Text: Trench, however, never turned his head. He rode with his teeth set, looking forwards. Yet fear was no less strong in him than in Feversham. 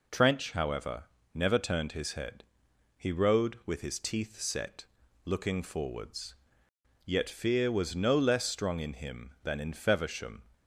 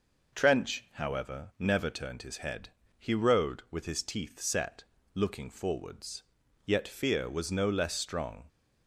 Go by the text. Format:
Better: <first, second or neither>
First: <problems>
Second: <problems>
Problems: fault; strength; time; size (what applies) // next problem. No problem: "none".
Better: first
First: none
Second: stops before "in him than in Feversham"; at 8.4 s